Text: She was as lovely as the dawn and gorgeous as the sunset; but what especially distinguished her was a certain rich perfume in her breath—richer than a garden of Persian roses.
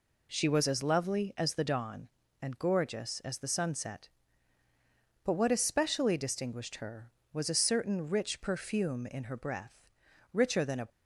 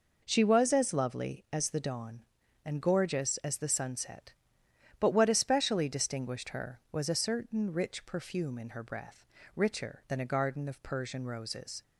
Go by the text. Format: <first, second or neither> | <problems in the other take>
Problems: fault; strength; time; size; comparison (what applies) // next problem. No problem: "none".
second | stops before "garden of Persian roses"; at 10.8 s